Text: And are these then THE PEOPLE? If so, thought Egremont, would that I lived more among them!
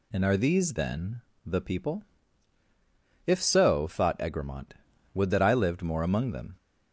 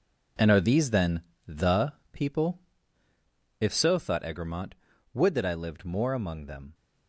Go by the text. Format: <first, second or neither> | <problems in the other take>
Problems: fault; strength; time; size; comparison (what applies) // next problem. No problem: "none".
first | gets quieter; strong; throughout; 10 dB // pauses between "then" and "THE"; slight; at 1.2 s; 0.26 s long; slight in the first // pauses between "THE" and "PEOPLE"; slight; at 1.9 s; 0.18 s long